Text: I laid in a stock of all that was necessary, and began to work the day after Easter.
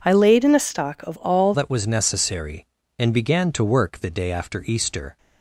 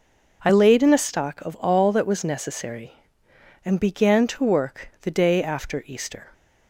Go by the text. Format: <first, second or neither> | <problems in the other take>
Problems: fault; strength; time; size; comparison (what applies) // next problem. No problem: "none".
second | changes voice at "that"; from 1.5 s on; 3.6 s long